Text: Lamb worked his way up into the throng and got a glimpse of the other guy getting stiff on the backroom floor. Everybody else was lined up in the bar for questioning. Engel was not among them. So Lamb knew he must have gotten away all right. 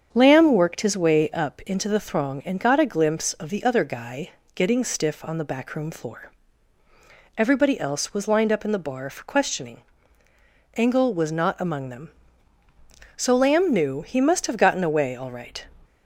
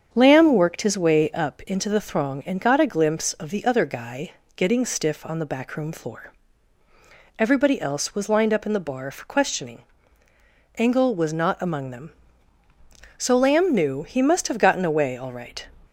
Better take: neither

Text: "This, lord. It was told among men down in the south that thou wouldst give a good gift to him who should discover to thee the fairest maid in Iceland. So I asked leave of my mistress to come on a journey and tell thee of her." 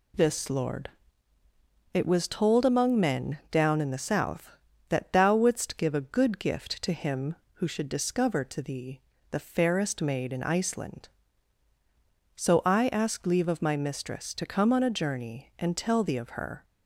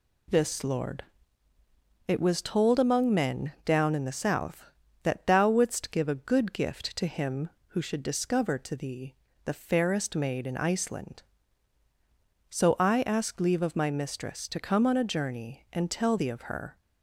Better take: neither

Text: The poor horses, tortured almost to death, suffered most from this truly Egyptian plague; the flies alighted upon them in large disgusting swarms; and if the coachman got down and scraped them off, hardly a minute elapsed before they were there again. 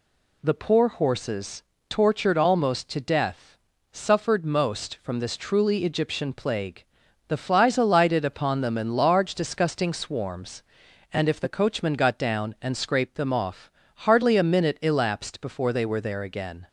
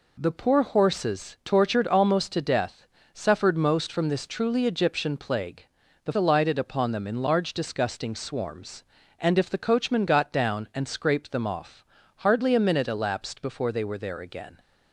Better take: first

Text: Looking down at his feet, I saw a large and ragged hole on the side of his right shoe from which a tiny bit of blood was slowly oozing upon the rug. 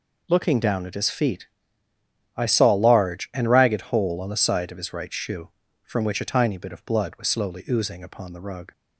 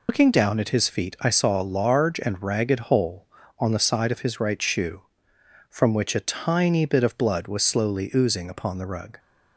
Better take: first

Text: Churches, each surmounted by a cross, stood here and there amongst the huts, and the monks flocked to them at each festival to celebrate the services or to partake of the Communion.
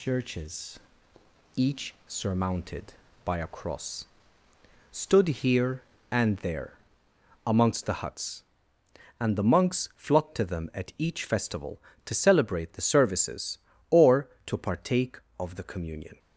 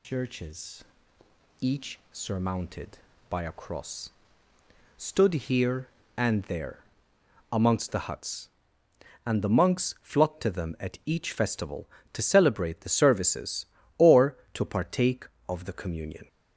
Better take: first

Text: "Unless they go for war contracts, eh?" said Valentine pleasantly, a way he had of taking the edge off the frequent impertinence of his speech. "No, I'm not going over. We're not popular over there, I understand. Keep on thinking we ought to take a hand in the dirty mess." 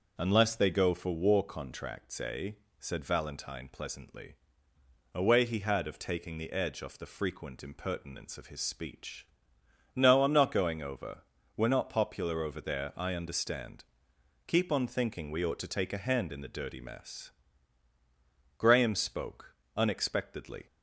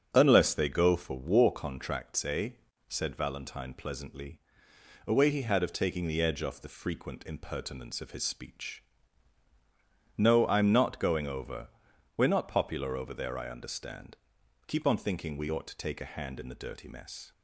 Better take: second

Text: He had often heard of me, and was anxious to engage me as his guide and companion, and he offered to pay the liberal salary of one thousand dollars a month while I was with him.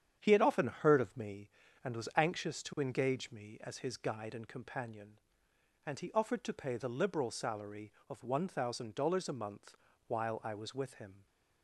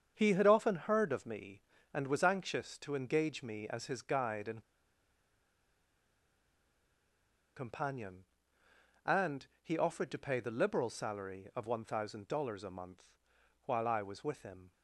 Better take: first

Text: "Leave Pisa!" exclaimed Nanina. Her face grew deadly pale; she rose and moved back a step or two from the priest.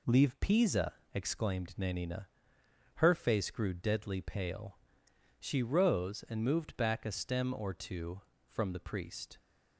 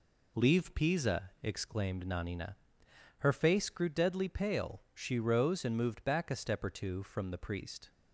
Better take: second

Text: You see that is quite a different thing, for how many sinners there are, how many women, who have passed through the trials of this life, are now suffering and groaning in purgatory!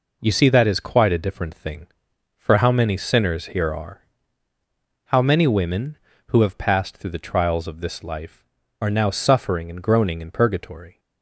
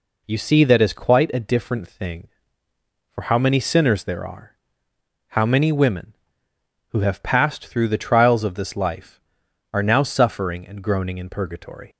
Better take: second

